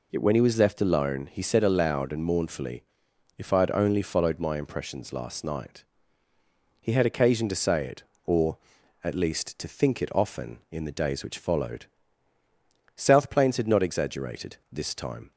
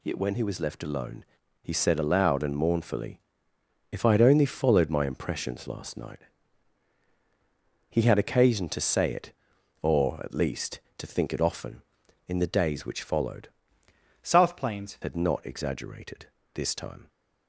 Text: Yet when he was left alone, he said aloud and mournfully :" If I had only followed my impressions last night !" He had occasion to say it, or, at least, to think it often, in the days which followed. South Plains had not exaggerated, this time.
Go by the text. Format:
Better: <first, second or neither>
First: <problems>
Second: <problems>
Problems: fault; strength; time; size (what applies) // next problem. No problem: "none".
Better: first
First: none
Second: changes voice from "South" to "Plains"; from 14.2 to 14.9 s; 0.7 s long